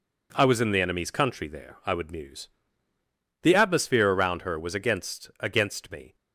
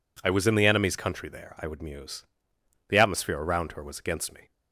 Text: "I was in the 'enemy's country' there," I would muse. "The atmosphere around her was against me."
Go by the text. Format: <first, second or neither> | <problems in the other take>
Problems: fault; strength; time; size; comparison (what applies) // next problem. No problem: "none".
second | says "against" twice; at 5.4 s